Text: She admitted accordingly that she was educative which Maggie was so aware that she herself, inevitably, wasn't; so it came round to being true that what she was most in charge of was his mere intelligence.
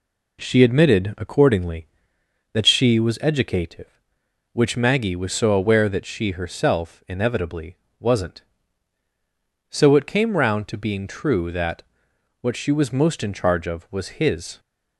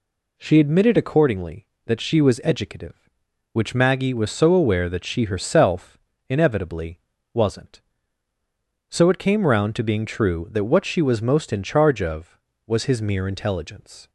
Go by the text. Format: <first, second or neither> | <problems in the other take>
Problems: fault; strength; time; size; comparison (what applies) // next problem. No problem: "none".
second | pauses between "that" and "what"; noticeable; at 11.8 s; 0.58 s long // stops before "mere intelligence"; at 14.5 s